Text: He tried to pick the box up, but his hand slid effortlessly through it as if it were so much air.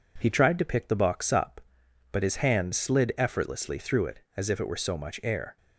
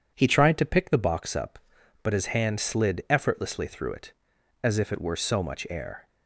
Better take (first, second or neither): neither